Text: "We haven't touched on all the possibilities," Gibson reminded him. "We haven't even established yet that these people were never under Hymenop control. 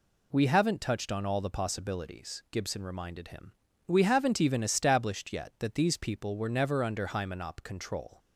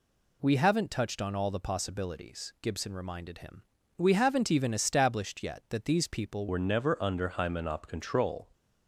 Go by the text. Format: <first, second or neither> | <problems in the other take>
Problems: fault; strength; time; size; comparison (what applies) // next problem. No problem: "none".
first | changes voice at "were"; from 6.4 s on; 2.0 s long